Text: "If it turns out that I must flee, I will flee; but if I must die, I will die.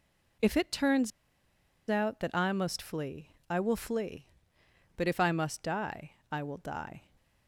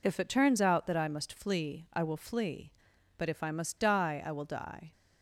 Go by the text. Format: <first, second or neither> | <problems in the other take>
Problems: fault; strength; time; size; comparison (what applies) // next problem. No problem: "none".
second | pauses between "turns" and "out"; noticeable; at 1.1 s; 0.80 s long